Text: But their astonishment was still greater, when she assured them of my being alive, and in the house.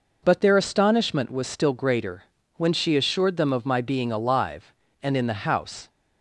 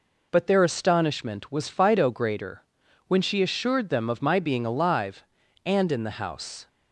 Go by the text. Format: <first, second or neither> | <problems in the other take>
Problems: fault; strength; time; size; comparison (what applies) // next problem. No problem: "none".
first | says "fido" for "still"; at 1.6 s